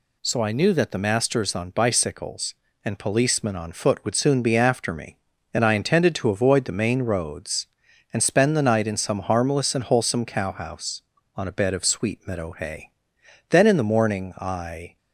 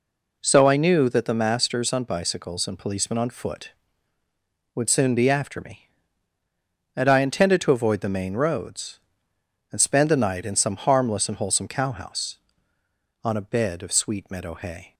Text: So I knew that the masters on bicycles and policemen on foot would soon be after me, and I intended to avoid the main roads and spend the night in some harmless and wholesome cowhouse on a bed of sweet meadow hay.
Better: second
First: goes on to say "Then in the morning I"; from 13.5 s on; 1.4 s long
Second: none

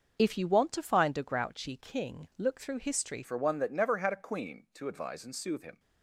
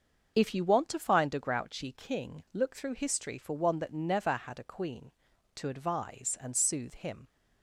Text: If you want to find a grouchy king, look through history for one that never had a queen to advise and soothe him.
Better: second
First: starts louder than the rest; noticeable; until 1.2 s; 6 dB // changes voice at "for"; from 3.2 s on; 2.5 s long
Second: starts louder than the rest; until 1.3 s; 6.5 dB

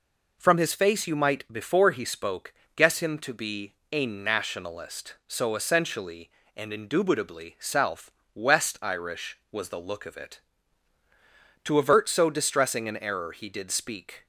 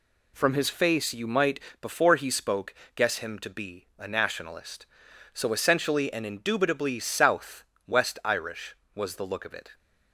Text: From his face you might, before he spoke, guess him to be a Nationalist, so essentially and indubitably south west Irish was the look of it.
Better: second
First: pauses between "be" and "a"; slight; at 3.7 s; 0.18 s long // pauses between "south" and "west"; slight; at 8.1 s; 0.24 s long // goes on to say "To avert so distressing an error he did speak"; strong; from 11.6 s on; 2.6 s long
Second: pauses between "south" and "west"; slight; at 7.6 s; 0.24 s long

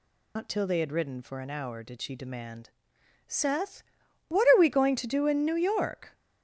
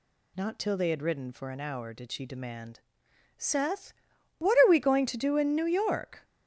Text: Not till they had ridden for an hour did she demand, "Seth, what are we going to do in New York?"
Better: second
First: loses the start of "Not"; at 0.3 s; 95 ms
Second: none

